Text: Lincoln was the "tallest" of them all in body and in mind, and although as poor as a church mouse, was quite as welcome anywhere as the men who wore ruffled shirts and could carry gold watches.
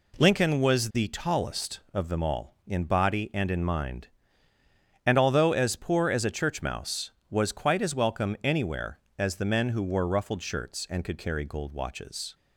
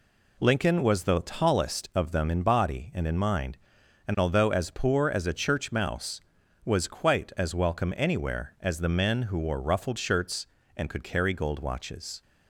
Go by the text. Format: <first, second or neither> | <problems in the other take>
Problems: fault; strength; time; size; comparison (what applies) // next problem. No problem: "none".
first | skips "all"; at 2.2 s